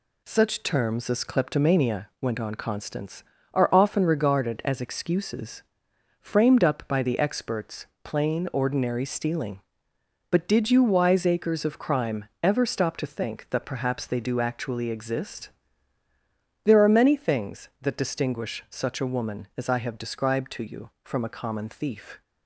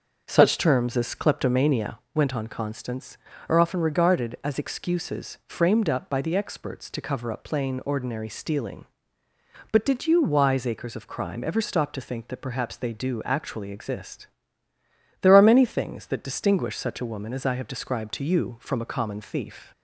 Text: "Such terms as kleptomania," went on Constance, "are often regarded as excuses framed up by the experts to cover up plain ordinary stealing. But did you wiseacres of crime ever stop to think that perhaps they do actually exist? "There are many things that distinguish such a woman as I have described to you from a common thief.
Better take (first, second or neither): second